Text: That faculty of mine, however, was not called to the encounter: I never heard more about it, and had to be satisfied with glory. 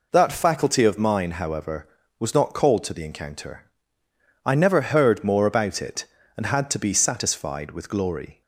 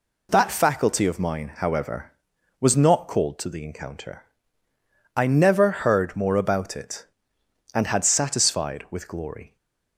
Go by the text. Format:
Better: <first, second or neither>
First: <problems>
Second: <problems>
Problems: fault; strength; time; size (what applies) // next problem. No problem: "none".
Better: first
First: none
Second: skips "to be"; at 8.0 s // stays silent after the last word; slight; from 9.4 s on; 0.5 s long